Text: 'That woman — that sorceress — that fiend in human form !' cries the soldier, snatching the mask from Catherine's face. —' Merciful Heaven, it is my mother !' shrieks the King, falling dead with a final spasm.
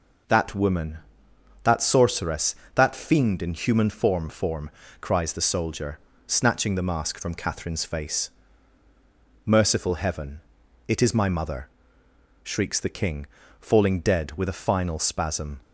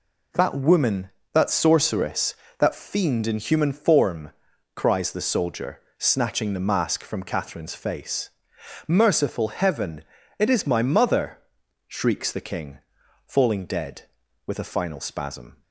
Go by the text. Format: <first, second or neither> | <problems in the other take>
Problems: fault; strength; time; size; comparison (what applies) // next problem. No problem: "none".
second | says "form" twice; at 4.2 s